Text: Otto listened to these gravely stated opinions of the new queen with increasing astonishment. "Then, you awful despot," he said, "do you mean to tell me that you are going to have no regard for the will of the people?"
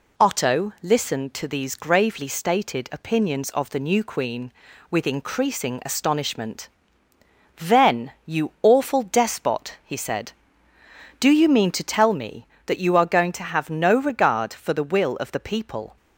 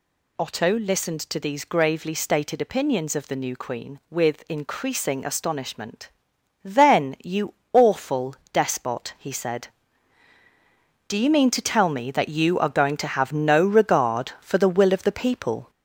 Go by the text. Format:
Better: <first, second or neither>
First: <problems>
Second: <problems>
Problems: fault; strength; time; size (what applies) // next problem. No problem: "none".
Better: first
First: none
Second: gets louder; noticeable; throughout; 4 dB // pauses between "you" and "awful"; slight; at 7.5 s; 0.18 s long // pauses between "awful" and "despot"; slight; at 8.3 s; 0.18 s long